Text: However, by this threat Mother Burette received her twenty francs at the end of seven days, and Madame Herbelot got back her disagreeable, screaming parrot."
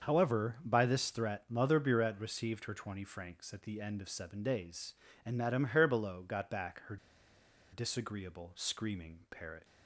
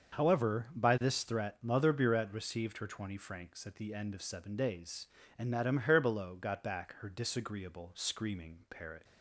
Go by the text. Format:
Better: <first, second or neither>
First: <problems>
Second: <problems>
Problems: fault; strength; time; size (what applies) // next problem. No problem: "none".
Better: second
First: starts louder than the rest; until 1.1 s; 6.5 dB // pauses between "her" and "disagreeable"; noticeable; at 6.9 s; 0.75 s long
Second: starts louder than the rest; until 1.2 s; 6.5 dB